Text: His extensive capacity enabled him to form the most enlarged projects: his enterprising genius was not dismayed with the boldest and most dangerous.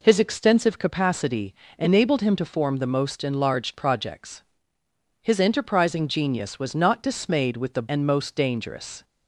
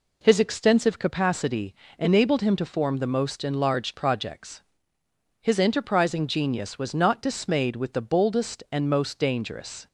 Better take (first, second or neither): second